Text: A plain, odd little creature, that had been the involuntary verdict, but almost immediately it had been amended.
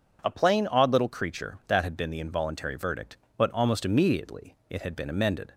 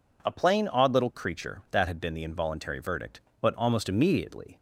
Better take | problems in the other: first | stops before "it had been amended"; at 4.5 s

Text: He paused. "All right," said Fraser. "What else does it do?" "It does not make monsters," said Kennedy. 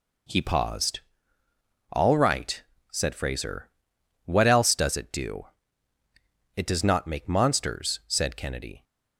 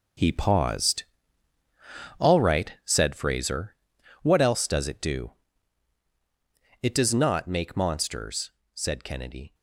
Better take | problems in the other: first | gets quieter; strong; throughout; 10 dB

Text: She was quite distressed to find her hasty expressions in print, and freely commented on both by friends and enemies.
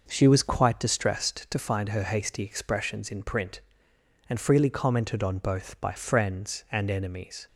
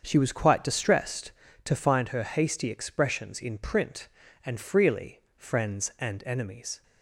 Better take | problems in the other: first | starts louder than the rest; until 1.0 s; 7 dB // skips "commented on both by"; at 5.3 s

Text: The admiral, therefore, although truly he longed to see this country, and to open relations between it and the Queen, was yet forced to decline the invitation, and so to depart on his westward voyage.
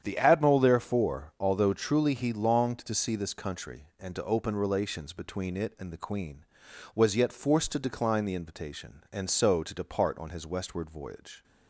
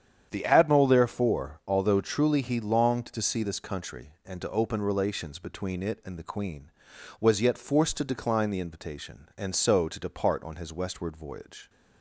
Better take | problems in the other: neither | starts louder than the rest; strong; the same in both

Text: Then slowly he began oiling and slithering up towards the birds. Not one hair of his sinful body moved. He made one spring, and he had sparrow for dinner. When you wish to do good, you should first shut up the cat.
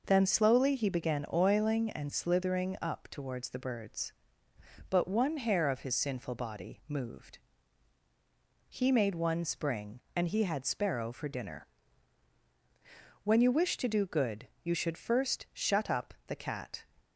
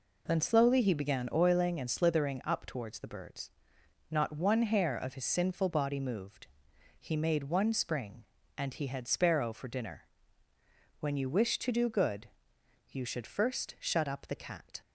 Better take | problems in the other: second | says "But" for "Not"; at 4.8 s

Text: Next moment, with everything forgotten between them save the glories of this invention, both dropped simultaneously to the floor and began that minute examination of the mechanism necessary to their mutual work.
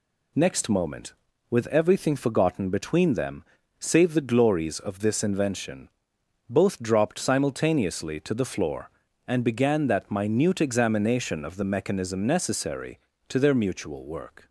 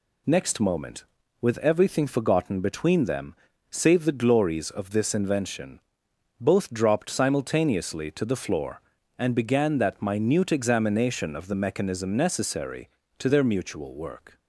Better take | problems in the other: neither | pauses between "them" and "save"; slight; the same in both

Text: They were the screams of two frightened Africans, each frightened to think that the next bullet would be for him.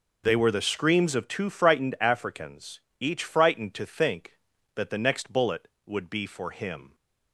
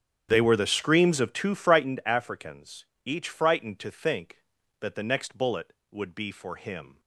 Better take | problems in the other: first | starts louder than the rest; strong; until 1.9 s; 9.5 dB

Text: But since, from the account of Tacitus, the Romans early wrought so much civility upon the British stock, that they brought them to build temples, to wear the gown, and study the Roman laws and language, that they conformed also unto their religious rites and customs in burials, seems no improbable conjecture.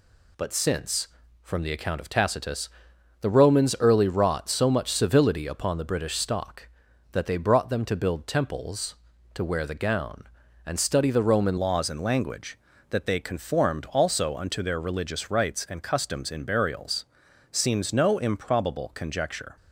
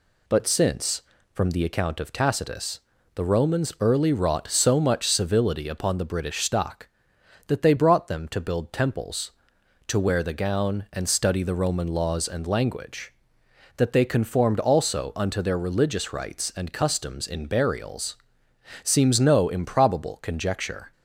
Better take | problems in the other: second | changes voice at "laws"; from 11.5 s on; 8.0 s long

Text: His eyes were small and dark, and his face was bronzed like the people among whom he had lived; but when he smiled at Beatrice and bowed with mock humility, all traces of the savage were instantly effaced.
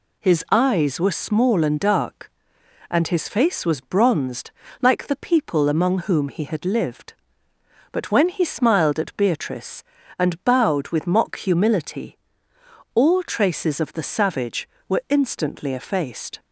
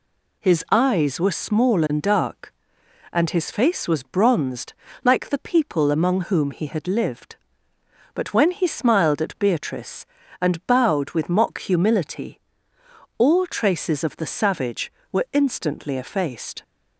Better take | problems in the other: neither | pauses between "bronzed" and "like"; slight; the same in both

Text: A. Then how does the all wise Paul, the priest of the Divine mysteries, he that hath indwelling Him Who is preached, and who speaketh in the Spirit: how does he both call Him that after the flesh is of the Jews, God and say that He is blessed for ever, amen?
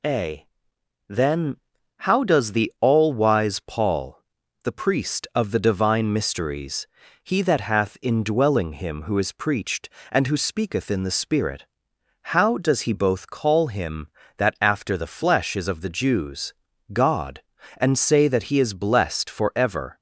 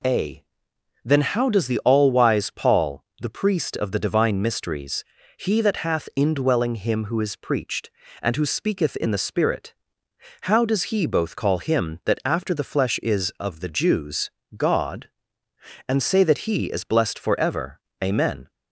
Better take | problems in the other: second | pauses between "Then" and "how"; noticeable; at 1.5 s; 0.48 s long // stops before "amen"; at 19.9 s

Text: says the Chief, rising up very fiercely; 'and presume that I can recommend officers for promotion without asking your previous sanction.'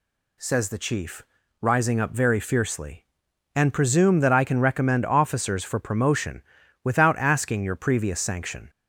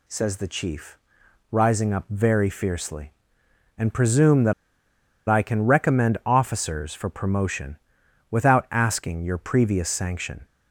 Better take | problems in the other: first | pauses between "that" and "I"; noticeable; at 4.5 s; 0.75 s long // pauses between "promotion" and "without"; noticeable; at 7.7 s; 0.54 s long; also in the first

